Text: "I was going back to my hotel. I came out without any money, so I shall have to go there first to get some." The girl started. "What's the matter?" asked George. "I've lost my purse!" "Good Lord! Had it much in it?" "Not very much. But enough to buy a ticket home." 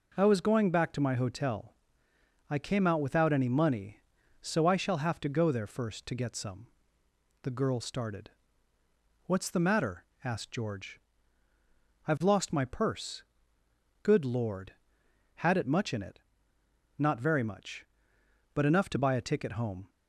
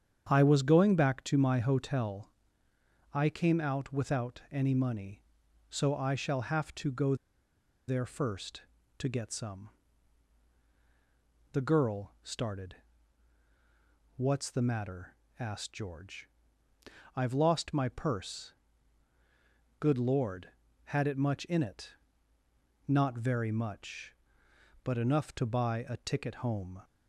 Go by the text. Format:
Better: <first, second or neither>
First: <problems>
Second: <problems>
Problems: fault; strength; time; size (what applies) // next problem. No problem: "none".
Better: first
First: none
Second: starts louder than the rest; strong; until 1.3 s; 8.5 dB // pauses between "go" and "there"; noticeable; at 7.1 s; 0.72 s long